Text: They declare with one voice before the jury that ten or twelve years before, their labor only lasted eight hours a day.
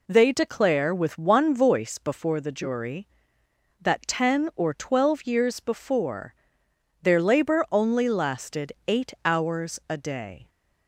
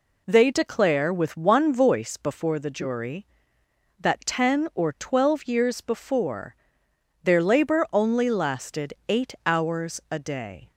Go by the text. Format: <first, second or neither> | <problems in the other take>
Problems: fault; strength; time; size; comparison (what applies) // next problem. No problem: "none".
neither | none